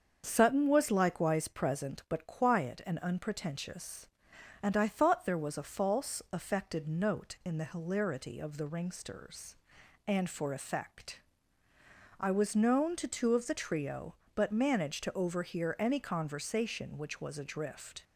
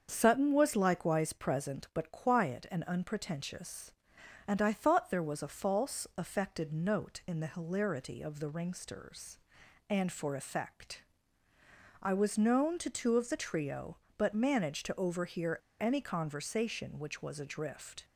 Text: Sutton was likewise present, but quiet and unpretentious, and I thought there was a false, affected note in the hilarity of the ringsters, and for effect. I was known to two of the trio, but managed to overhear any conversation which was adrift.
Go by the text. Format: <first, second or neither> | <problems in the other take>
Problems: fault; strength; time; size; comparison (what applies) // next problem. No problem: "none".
first | starts louder than the rest; until 1.1 s; 7 dB; also in the first // pauses between "overhear" and "any"; slight; at 15.5 s; 0.21 s long